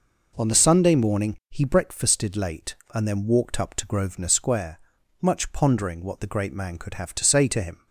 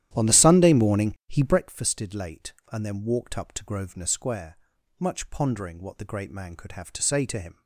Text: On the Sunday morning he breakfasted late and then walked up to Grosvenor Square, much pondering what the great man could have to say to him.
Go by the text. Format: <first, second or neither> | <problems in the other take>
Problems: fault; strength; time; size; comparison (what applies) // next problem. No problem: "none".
first | starts louder than the rest; strong; until 1.7 s; 12 dB